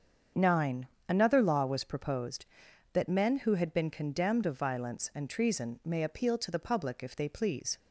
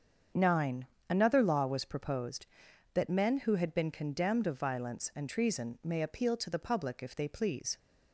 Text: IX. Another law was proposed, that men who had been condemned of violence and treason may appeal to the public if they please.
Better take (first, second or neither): neither